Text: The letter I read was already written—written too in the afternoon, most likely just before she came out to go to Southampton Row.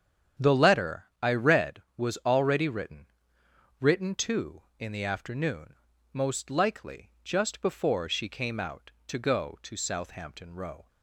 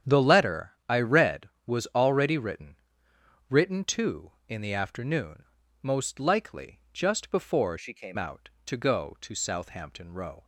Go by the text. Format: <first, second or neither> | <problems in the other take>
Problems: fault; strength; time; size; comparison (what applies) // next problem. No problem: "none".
first | starts louder than the rest; strong; until 1.1 s; 9 dB; strong in the first // changes voice from "she" to "came"; from 7.7 to 8.1 s; 0.4 s long